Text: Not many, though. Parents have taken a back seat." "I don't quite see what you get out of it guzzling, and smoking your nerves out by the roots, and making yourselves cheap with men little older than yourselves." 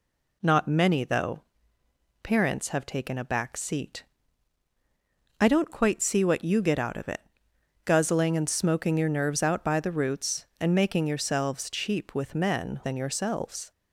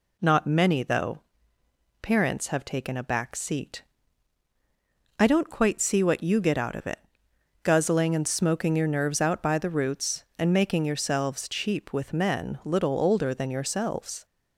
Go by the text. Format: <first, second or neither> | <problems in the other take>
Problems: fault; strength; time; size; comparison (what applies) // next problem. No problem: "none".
second | pauses between "it" and "guzzling"; noticeable; at 7.1 s; 0.64 s long; noticeable in the second // skips "little older"; at 12.8 s